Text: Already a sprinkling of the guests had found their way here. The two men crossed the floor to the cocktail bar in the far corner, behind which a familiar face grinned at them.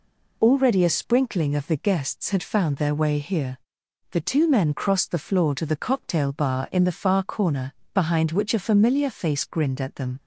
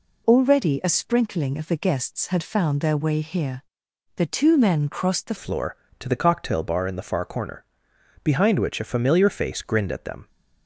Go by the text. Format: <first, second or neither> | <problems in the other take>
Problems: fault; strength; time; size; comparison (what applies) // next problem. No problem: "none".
first | changes voice at "floor"; from 5.3 s on; 4.9 s long